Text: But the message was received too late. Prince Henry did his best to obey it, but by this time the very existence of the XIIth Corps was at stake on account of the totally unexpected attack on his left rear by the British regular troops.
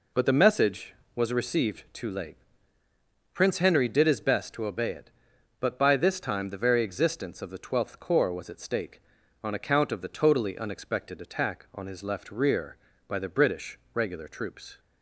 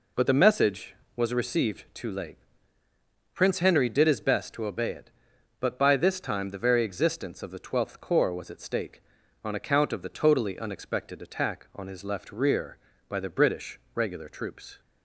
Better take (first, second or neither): neither